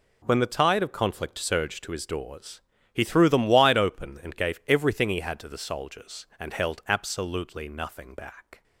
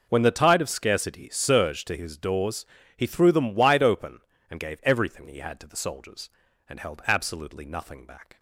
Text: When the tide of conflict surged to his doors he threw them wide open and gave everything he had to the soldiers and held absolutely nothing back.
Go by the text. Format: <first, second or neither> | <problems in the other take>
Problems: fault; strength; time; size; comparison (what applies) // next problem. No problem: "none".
first | says "scarcity" for "conflict"; at 0.7 s // pauses between "doors" and "he"; slight; at 2.6 s; 0.32 s long; slight in the first